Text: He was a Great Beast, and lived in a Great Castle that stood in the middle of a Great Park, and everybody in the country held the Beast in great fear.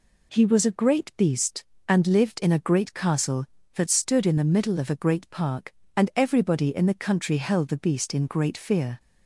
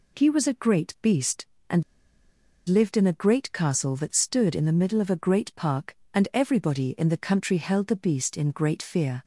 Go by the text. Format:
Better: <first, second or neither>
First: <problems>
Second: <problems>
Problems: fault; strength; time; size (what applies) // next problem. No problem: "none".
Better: first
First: none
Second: pauses between "and" and "lived"; noticeable; at 1.8 s; 0.84 s long